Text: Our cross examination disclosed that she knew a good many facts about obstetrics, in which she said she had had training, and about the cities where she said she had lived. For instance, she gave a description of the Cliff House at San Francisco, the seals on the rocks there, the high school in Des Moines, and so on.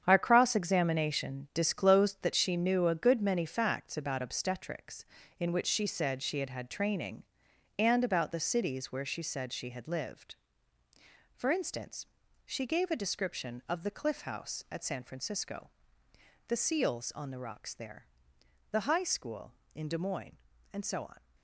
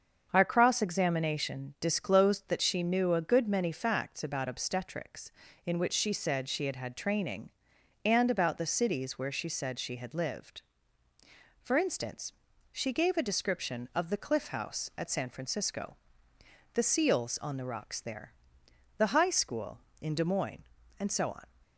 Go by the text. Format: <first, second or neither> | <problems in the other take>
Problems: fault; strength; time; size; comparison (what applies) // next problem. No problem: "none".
second | gets quieter; strong; throughout; 10 dB // starts louder than the rest; strong; until 1.0 s; 8.5 dB; also in the second